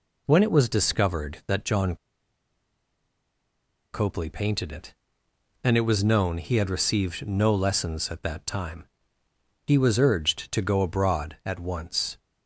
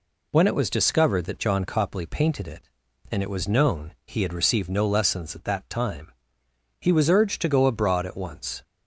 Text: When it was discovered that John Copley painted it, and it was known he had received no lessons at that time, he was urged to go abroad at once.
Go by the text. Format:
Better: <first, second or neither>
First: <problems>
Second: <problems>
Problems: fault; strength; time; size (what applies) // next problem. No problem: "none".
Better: second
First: pauses between "John" and "Copley"; strong; at 1.9 s; 1.9 s long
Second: none